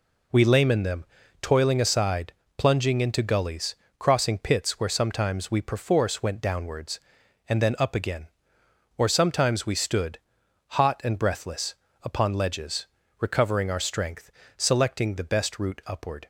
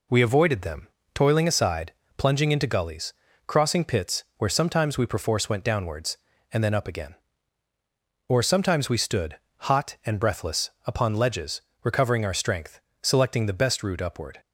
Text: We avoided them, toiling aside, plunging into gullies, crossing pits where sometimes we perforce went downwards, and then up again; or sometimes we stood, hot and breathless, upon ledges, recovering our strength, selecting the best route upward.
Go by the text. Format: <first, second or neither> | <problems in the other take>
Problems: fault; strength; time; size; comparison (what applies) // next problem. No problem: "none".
second | says "layman" for "avoided"; at 0.4 s